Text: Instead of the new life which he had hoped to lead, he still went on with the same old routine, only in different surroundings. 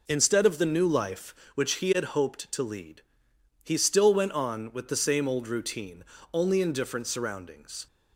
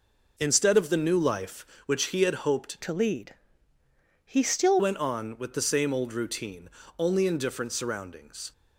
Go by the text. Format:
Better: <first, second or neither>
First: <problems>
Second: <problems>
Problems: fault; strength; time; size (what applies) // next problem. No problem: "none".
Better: first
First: none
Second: changes voice from "to" to "still"; from 2.8 to 4.7 s; 1.9 s long